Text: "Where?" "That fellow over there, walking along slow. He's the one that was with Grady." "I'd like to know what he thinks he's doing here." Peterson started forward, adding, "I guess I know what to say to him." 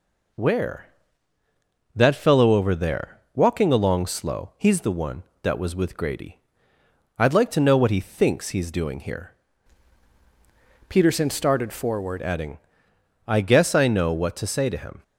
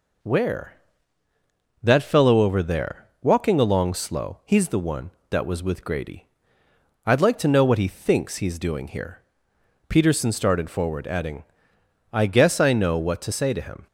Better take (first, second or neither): second